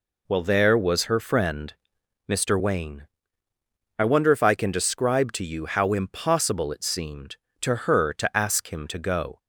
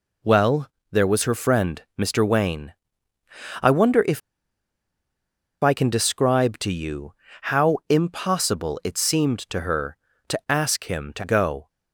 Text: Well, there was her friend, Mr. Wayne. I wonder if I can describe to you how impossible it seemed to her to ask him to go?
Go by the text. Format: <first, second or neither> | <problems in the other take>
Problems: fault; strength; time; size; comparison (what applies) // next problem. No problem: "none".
first | pauses between "if" and "I"; strong; at 4.2 s; 1.4 s long // pauses between "you" and "how"; slight; at 7.1 s; 0.30 s long